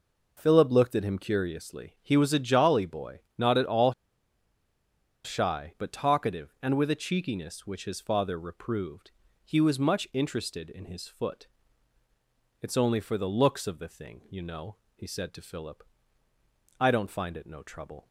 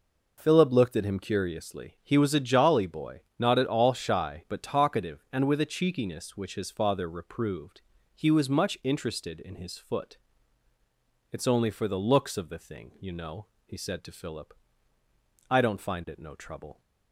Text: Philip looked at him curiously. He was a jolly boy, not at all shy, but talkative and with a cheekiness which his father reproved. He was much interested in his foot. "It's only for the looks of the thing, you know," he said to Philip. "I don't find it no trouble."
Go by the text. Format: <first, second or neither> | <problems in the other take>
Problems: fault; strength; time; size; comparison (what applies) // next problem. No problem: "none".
second | pauses between "all" and "shy"; strong; at 3.9 s; 1.3 s long